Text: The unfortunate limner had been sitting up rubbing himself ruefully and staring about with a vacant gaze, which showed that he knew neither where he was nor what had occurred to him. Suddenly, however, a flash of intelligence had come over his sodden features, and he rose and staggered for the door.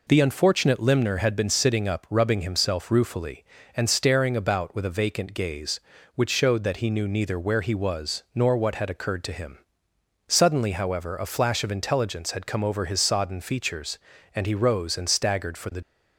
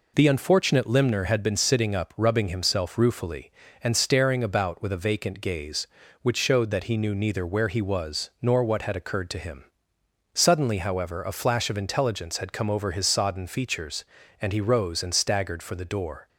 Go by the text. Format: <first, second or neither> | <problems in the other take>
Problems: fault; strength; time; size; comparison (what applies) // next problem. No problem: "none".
second | stops before "door"; at 15.8 s